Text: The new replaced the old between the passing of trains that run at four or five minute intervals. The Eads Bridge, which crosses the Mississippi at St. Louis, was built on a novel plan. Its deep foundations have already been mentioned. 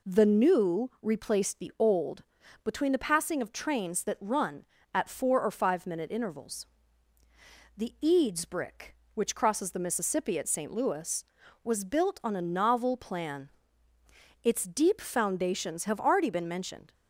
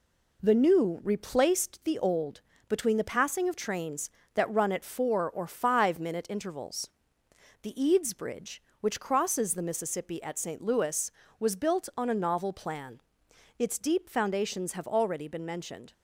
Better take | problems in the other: second | pauses between "old" and "between"; at 2.2 s; 0.42 s long; slight in the second // says "Brick" for "Bridge"; at 8.4 s

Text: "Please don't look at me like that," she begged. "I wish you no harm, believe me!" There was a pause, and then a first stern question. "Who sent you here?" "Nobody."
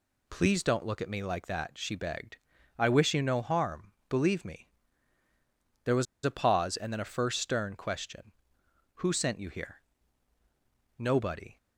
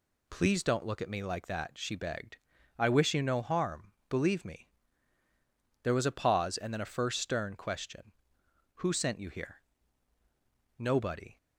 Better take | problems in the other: second | pauses between "was" and "a"; slight; at 6.0 s; 0.19 s long

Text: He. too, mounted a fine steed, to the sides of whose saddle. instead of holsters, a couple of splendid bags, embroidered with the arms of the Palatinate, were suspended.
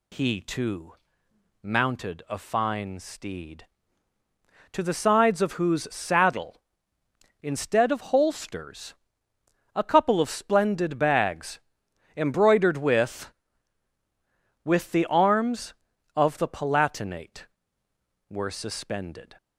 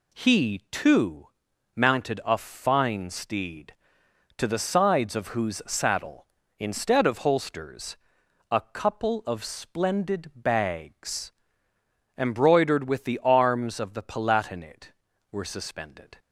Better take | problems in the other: second | says "with" twice; at 14.6 s

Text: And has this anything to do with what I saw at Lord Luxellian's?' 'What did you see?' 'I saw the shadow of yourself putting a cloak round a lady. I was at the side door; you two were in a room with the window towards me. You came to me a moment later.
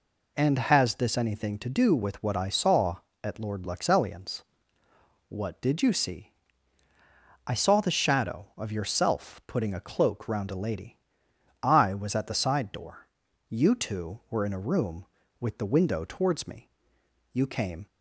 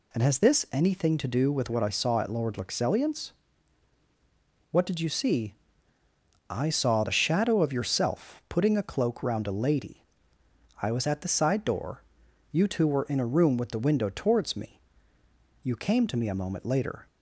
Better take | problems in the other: second | stops before "to me a moment later"; at 17.8 s

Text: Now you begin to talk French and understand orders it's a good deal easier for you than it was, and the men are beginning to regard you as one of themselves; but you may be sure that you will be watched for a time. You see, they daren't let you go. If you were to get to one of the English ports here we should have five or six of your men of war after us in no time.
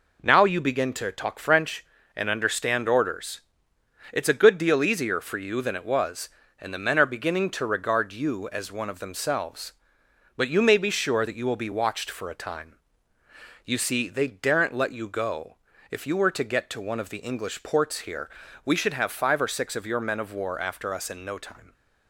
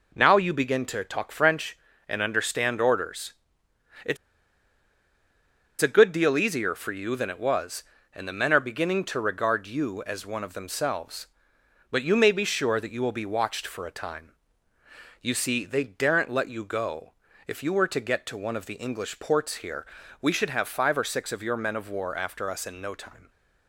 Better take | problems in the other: first | pauses between "orders" and "it's"; noticeable; at 3.3 s; 0.72 s long; noticeable in the first // pauses between "it's" and "a"; strong; at 4.1 s; 1.6 s long // pauses between "here" and "we"; at 19.8 s; 0.38 s long; also in the first

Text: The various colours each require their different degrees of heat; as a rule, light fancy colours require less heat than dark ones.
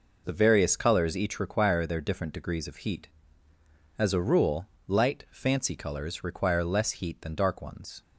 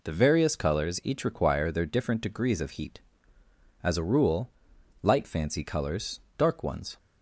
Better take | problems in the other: first | skips "require less heat than"; at 6.2 s

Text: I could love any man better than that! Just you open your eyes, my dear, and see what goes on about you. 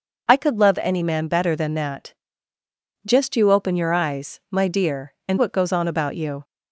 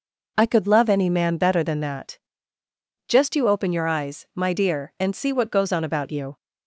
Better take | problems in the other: second | skips "see"; at 5.3 s

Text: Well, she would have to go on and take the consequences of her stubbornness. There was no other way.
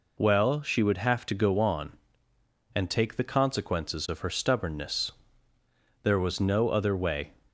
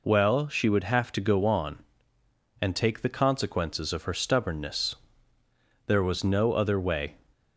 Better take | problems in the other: neither | none

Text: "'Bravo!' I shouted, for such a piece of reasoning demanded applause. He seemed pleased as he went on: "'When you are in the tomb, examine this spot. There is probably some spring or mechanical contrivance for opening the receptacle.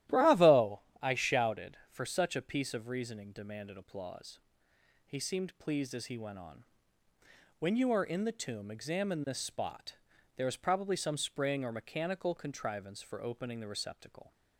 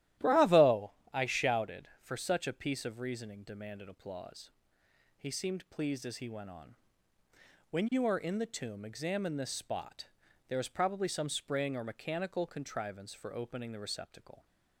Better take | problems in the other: neither | starts louder than the rest; strong; the same in both

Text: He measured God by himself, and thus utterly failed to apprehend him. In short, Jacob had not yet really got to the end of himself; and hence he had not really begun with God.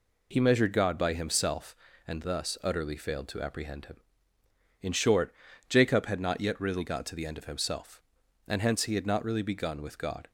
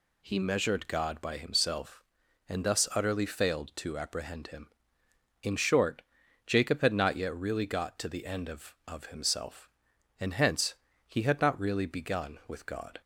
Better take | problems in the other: first | says "of" twice; at 8.8 s // pauses between "hence" and "he"; slight; at 10.7 s; 0.34 s long

